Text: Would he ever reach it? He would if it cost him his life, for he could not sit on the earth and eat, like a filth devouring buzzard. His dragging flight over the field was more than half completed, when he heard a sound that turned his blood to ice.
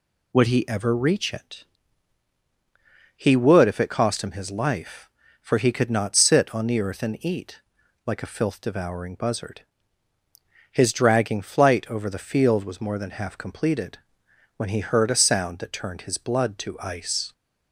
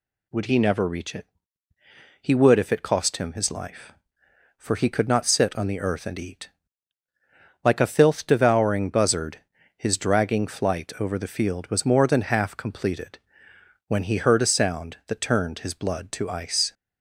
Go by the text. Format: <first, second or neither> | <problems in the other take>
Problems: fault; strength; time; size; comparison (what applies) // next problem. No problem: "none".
first | says "never" for "ever"; at 0.5 s